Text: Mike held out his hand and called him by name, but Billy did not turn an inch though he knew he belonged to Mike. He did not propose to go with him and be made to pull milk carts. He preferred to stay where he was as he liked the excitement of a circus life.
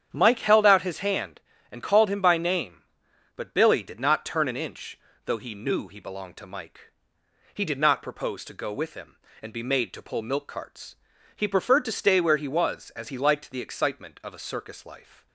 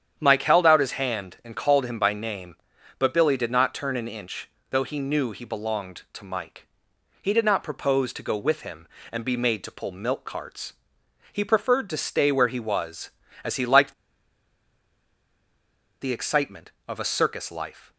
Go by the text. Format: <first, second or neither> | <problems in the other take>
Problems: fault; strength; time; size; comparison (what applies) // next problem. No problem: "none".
first | starts louder than the rest; strong; until 1.1 s; 9 dB; strong in the first // pauses between "inch" and "though"; slight; at 4.4 s; 0.22 s long; slight in the first // pauses between "liked" and "the"; strong; at 13.9 s; 2.0 s long